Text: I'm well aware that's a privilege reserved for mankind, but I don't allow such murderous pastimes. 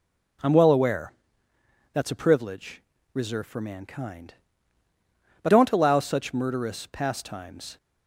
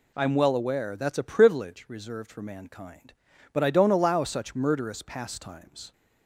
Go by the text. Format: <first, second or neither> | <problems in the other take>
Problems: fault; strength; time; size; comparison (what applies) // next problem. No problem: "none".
second | pauses between "aware" and "that's"; noticeable; at 1.1 s; 0.80 s long // pauses between "privilege" and "reserved"; slight; at 2.8 s; 0.30 s long // skips "I"; at 5.4 s